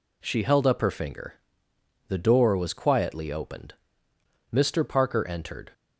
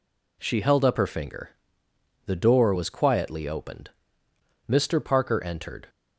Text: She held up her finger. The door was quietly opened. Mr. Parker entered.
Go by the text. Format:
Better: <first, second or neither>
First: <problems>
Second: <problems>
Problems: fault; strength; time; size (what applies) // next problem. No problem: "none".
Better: neither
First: none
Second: none